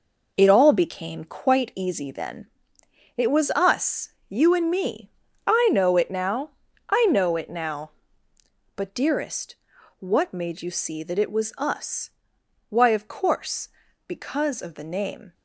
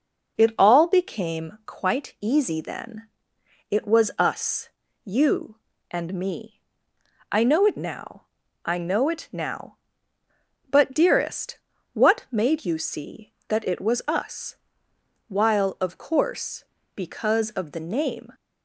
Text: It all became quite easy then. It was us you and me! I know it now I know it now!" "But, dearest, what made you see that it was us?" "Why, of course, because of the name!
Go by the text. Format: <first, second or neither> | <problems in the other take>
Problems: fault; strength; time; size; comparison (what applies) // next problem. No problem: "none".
first | pauses between "us" and "you"; slight; at 4.6 s; 0.36 s long; slight in the first // pauses between "now" and "I"; at 8.2 s; 0.44 s long; also in the first // says "While" for "Why"; at 15.2 s